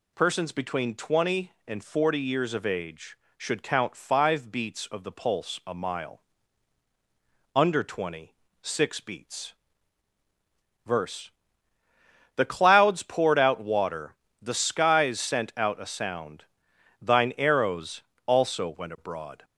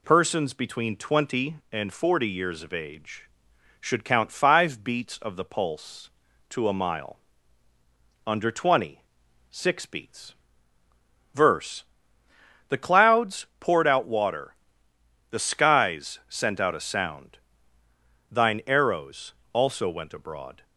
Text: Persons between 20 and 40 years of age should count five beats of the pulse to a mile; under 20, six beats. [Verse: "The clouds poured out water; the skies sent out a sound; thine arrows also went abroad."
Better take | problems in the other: second | skips "to"; at 5.6 s // pauses between "arrows" and "also"; slight; at 18.0 s; 0.24 s long; slight in the second

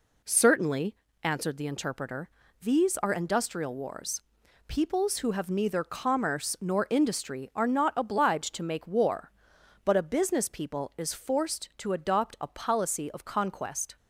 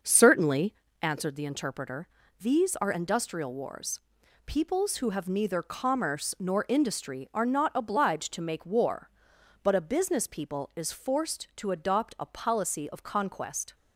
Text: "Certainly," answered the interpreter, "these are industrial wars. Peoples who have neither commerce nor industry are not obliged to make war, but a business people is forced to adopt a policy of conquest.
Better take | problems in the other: first | starts louder than the rest; noticeable; until 1.1 s; 6 dB

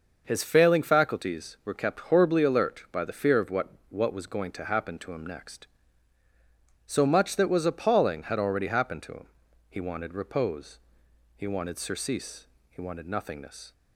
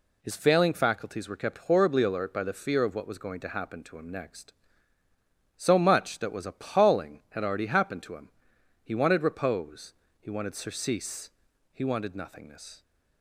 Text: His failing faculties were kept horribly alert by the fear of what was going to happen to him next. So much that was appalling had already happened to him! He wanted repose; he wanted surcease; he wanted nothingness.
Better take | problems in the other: second | starts louder than the rest; noticeable; until 1.2 s; 6 dB // says "what" twice; at 3.8 s

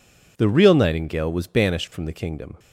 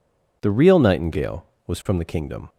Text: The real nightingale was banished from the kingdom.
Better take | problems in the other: first | skips "banished"; at 1.8 s

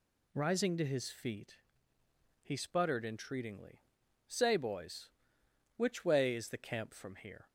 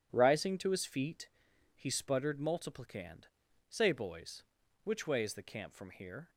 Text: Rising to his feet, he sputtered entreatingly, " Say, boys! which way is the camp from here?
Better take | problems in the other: first | starts louder than the rest; until 1.1 s; 6.5 dB // says "multiplicand" for "entreatingly"; at 2.3 s

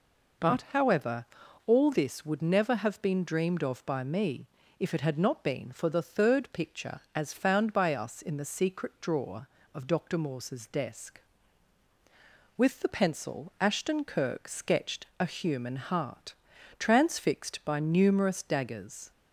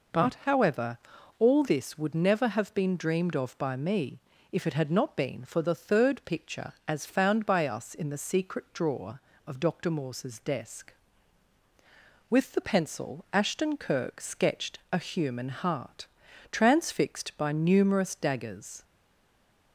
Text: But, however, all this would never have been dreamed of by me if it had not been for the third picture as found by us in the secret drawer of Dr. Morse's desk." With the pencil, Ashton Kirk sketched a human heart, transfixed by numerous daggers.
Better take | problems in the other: first | pauses between "me" and "if"; slight; at 4.1 s; 0.32 s long; slight in the first // stays silent after the last word; slight; from 18.8 s on; 0.9 s long

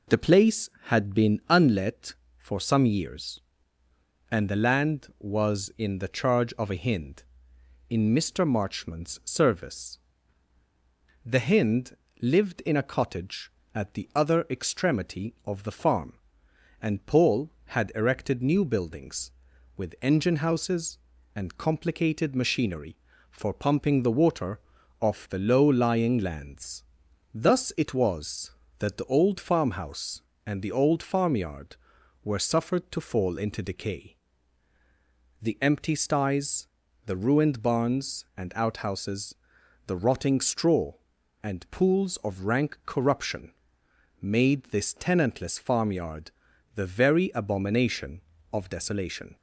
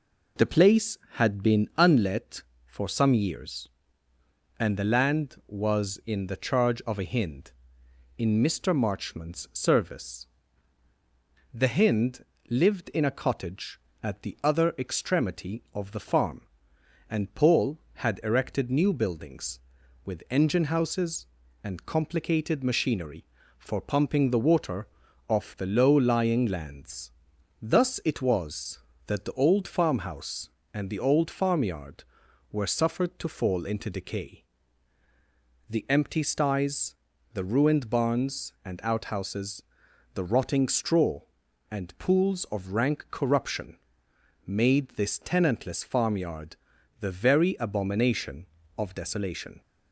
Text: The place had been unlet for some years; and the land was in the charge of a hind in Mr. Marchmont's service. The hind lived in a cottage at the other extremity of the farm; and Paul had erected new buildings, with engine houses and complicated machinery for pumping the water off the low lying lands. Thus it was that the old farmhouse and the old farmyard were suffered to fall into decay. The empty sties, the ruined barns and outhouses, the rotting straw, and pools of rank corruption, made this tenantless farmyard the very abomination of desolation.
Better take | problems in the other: neither | pauses between "hind" and "lived"; slight; the same in both // pauses between "water" and "off"; the same in both // pauses between "farmyard" and "the"; the same in both

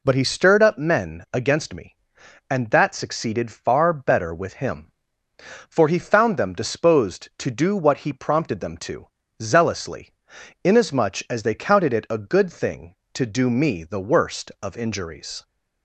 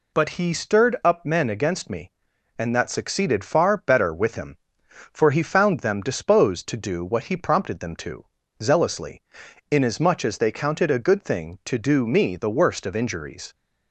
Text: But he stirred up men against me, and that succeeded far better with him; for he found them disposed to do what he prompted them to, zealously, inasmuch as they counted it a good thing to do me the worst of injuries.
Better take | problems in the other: first | skips "it"; at 10.9 s

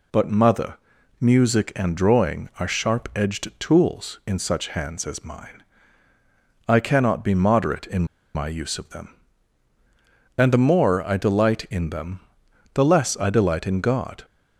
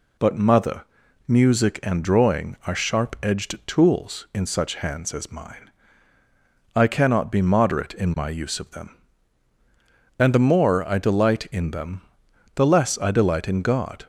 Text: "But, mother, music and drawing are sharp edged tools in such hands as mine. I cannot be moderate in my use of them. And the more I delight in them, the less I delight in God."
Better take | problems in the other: second | pauses between "in" and "my"; slight; at 8.0 s; 0.30 s long

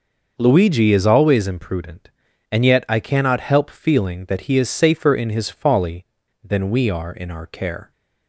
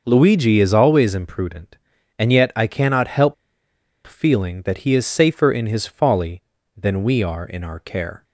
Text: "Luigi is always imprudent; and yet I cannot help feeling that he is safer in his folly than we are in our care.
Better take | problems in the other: first | pauses between "help" and "feeling"; noticeable; at 3.3 s; 0.72 s long

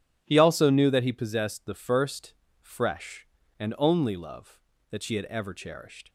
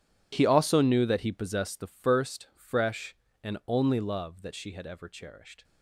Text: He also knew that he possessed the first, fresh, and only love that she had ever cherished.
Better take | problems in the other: first | gets quieter; strong; throughout; 17 dB

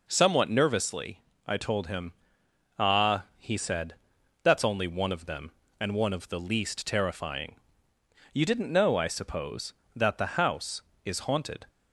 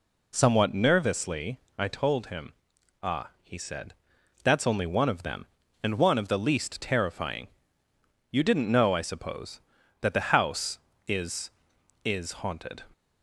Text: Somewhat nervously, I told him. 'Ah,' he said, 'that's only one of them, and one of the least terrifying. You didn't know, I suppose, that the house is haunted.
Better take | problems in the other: first | says "is" twice; at 12.0 s

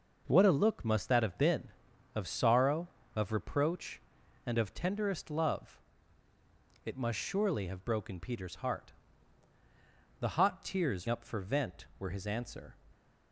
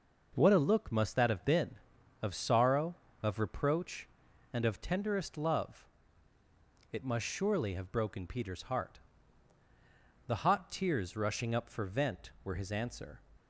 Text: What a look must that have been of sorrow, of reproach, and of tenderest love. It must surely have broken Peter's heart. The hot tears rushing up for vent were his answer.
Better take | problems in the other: second | skips "rushing"; at 11.0 s

